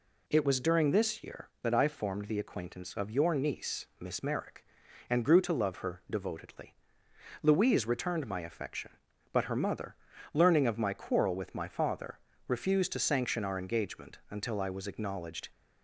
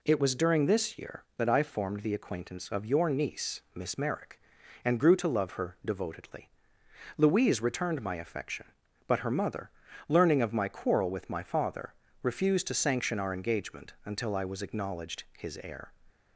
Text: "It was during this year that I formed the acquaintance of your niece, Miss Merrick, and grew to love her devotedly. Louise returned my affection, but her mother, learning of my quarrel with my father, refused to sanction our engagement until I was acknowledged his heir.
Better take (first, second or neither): second